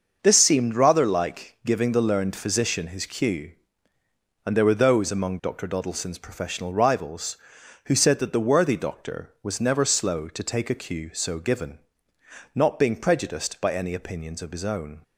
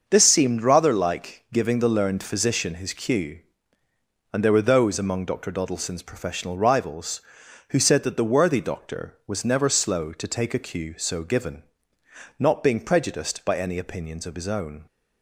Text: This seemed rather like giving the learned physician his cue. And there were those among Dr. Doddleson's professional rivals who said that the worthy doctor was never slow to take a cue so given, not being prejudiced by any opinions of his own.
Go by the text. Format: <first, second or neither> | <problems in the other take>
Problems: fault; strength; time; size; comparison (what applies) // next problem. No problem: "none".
neither | starts louder than the rest; the same in both